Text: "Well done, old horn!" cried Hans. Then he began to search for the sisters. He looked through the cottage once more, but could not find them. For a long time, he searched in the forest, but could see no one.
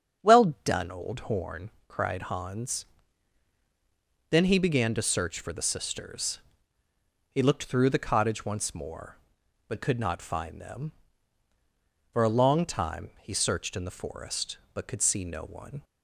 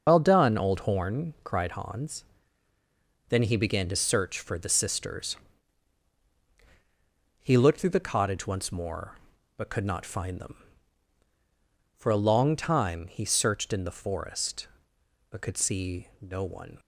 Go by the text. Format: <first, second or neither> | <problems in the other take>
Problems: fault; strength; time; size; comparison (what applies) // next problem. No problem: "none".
first | loses the start of "Well"; at 0.0 s; 95 ms // starts louder than the rest; until 1.0 s; 6 dB; strong in the first